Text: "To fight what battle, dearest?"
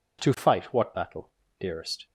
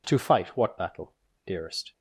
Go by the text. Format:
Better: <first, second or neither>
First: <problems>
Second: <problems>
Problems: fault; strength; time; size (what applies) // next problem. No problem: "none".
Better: neither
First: none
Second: none